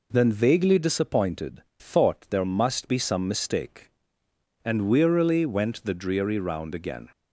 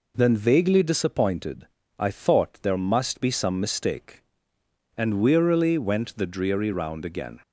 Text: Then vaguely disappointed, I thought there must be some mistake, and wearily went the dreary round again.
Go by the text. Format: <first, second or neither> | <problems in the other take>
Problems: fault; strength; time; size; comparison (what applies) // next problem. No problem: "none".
second | skips "I"; at 1.7 s